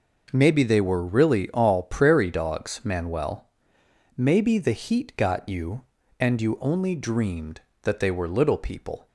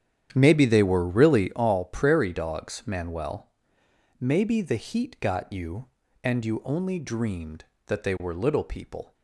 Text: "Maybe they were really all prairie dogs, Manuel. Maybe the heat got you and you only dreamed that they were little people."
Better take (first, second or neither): first